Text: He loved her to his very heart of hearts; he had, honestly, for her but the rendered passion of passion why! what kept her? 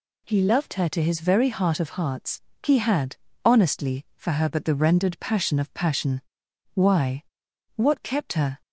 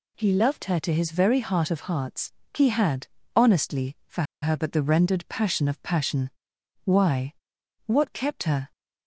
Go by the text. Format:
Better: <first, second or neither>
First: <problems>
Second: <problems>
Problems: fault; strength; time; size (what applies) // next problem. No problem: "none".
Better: first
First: pauses between "passion" and "why"; noticeable; at 6.2 s; 0.52 s long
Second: pauses between "for" and "her"; slight; at 4.2 s; 0.19 s long // pauses between "passion" and "why"; noticeable; at 6.2 s; 0.54 s long